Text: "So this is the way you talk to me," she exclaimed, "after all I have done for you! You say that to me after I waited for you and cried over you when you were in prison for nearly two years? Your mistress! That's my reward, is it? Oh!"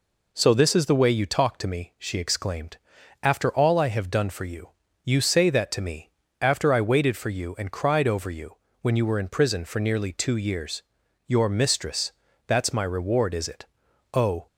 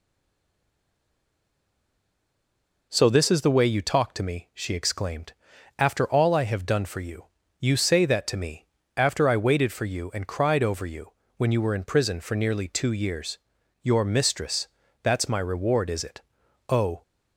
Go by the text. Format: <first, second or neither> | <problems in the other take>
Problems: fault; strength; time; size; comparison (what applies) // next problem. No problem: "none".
first | stays silent before the first word; strong; until 2.8 s; 2.8 s long // pauses between "me" and "after"; slight; at 8.6 s; 0.32 s long; slight in the first // pauses between "you" and "when"; slight; at 11.1 s; 0.24 s long; slight in the first